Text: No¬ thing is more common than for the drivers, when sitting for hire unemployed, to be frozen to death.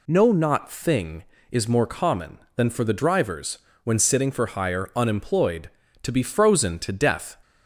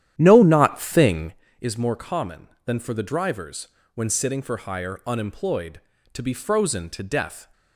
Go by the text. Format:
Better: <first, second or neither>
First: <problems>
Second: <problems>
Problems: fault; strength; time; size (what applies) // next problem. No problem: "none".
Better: first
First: none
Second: starts louder than the rest; strong; until 1.4 s; 11 dB